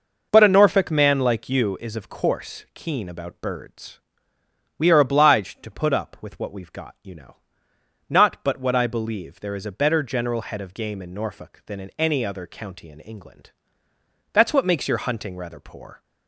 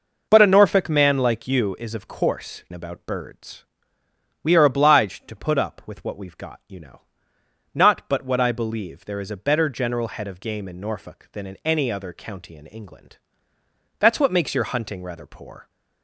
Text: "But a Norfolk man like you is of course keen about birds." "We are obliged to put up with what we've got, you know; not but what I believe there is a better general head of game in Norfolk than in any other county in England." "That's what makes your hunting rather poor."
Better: first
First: none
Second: skips "keen"; at 2.6 s

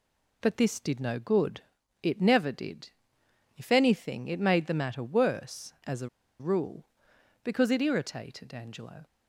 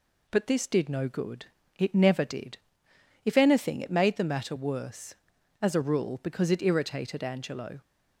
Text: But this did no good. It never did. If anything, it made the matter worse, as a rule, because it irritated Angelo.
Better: second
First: pauses between "a" and "rule"; slight; at 6.0 s; 0.31 s long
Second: none

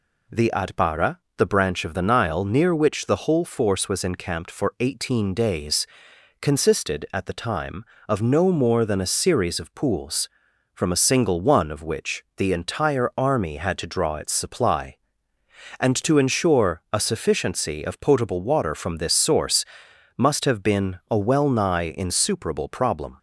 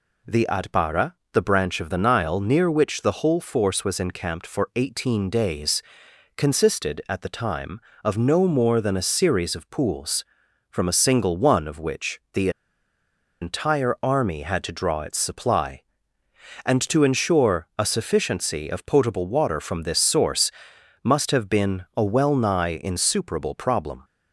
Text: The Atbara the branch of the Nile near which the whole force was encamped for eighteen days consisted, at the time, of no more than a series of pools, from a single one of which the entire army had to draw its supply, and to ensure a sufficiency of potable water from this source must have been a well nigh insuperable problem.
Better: first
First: pauses between "Atbara" and "the"; slight; at 1.1 s; 0.20 s long // pauses between "days" and "consisted"; noticeable; at 5.8 s; 0.54 s long // pauses between "source" and "must"; noticeable; at 19.6 s; 0.52 s long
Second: pauses between "Atbara" and "the"; slight; at 1.1 s; 0.20 s long // pauses between "days" and "consisted"; noticeable; at 5.8 s; 0.54 s long // pauses between "the" and "entire"; noticeable; at 12.4 s; 0.92 s long // pauses between "source" and "must"; noticeable; at 20.5 s; 0.52 s long

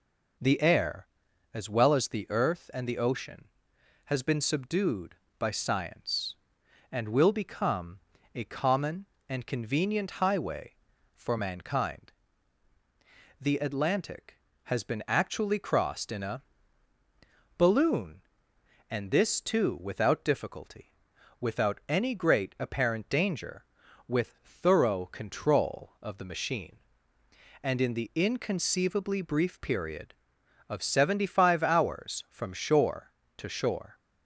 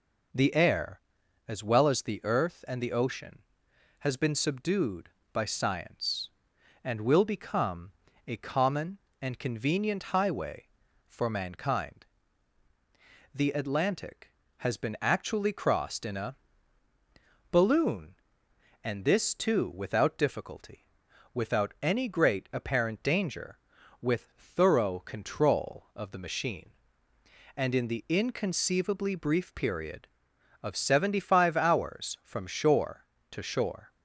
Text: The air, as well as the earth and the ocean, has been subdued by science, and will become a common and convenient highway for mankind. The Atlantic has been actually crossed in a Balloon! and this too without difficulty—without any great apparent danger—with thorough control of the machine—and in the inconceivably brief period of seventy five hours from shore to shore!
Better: neither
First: pauses between "become" and "a"; slight; at 8.0 s; 0.34 s long // pauses between "a" and "Balloon"; at 16.4 s; 1.1 s long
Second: pauses between "become" and "a"; slight; at 7.9 s; 0.34 s long // pauses between "a" and "Balloon"; at 16.3 s; 1.1 s long

